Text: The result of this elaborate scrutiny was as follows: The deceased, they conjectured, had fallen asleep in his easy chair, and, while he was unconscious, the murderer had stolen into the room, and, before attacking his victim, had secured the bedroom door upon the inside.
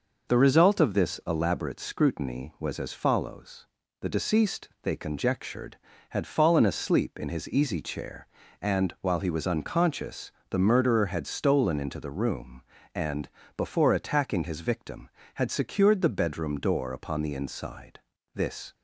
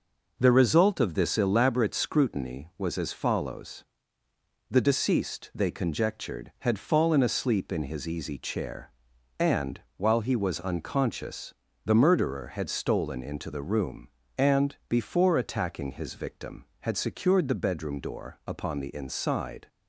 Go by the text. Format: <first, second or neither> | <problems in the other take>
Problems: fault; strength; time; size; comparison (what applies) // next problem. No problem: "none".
second | goes on to say "This"; slight; from 18.3 s on; 0.38 s long